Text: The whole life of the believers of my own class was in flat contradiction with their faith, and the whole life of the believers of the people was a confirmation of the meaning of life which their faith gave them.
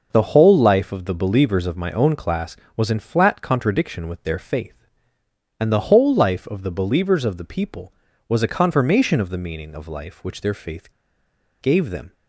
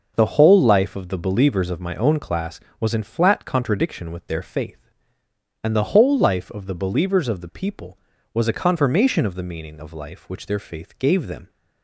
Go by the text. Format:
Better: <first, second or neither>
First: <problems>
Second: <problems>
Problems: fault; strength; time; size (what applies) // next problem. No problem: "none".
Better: second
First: starts louder than the rest; noticeable; until 1.1 s; 6 dB // pauses between "faith" and "gave"; noticeable; at 10.9 s; 0.70 s long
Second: starts louder than the rest; noticeable; until 1.1 s; 6 dB